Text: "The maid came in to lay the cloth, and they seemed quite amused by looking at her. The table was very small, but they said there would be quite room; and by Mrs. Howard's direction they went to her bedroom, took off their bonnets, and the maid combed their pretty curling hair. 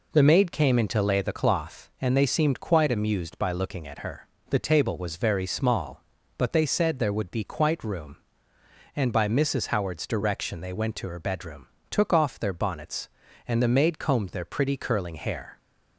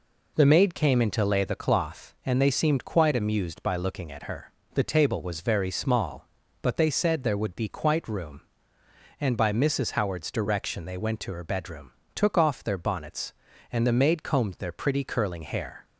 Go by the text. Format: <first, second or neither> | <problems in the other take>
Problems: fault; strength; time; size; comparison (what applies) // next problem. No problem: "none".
neither | none